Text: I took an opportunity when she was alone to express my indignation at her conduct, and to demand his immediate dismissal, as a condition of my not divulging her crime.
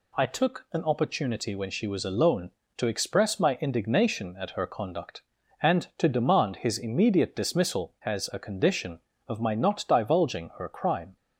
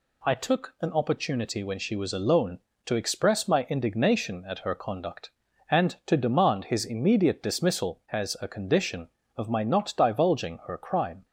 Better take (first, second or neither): neither